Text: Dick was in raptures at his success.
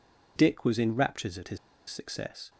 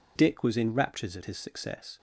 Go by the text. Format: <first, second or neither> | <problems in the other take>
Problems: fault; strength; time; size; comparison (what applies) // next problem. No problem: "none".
second | pauses between "his" and "success"; slight; at 1.5 s; 0.31 s long